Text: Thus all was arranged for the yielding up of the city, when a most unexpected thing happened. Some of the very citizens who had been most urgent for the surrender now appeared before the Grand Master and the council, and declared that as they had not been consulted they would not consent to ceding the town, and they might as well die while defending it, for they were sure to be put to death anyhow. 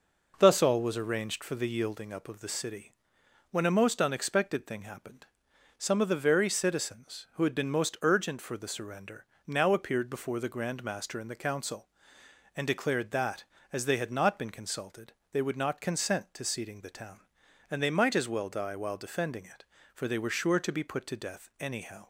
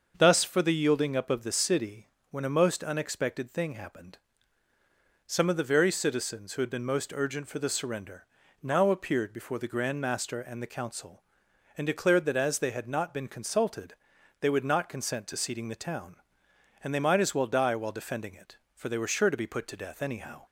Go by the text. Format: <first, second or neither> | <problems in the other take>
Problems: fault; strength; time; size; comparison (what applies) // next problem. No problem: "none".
first | starts louder than the rest; until 1.1 s; 6.5 dB // skips "all was arranged"; at 0.4 s // pauses between "surrender" and "now"; at 8.2 s; 0.38 s long; slight in the first // pauses between "consulted" and "they"; at 13.9 s; 0.44 s long; slight in the first